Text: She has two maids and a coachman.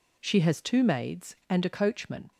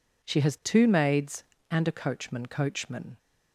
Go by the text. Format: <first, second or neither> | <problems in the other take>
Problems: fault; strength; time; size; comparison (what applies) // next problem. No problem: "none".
first | says "coachman" twice; at 2.4 s